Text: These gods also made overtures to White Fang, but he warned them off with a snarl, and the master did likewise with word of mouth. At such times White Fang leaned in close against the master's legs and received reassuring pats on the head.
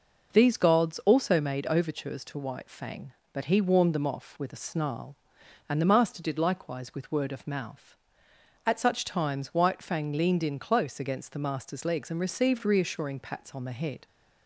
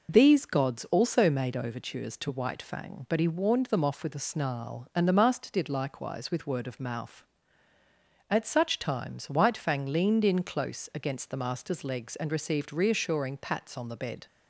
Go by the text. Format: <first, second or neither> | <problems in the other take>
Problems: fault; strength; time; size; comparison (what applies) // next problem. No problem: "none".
first | says "bed" for "head"; at 13.9 s